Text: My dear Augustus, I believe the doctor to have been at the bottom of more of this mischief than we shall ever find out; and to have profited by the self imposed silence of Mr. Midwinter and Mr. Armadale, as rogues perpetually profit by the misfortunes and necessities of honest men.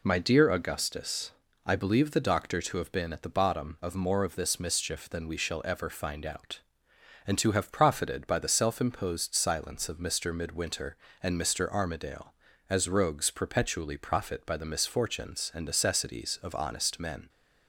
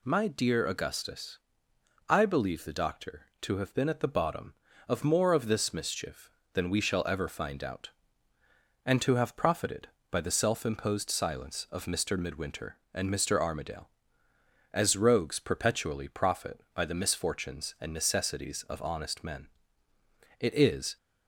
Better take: first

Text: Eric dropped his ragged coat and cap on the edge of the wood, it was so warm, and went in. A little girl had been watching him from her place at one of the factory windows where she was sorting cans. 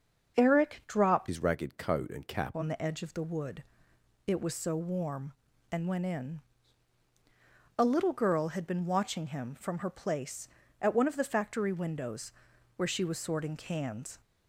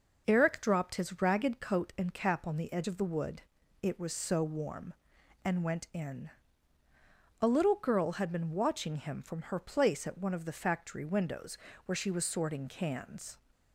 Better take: second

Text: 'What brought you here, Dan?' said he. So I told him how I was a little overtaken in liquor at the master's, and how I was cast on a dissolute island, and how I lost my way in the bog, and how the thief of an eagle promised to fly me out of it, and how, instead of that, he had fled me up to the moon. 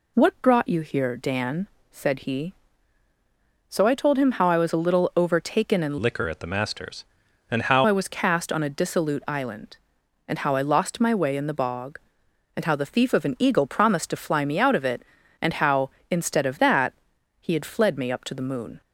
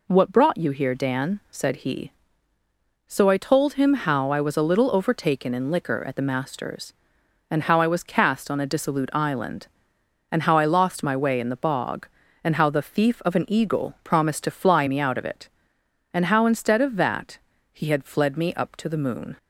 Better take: second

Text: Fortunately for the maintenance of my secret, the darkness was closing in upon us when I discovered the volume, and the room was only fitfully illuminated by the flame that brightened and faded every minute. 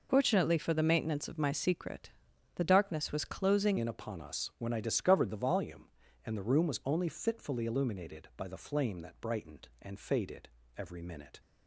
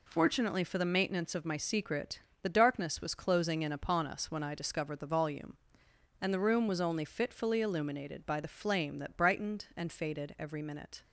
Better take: second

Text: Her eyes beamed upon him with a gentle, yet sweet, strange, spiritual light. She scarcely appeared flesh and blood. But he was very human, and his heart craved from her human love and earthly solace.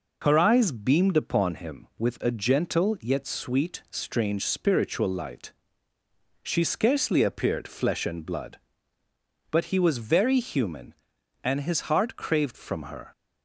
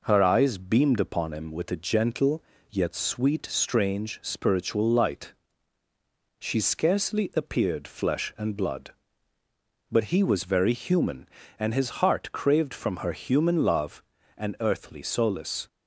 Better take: second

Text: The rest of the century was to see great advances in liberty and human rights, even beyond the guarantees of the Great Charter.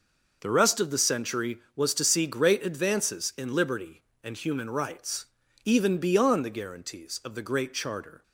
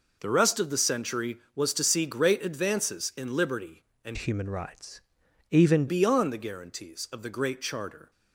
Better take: first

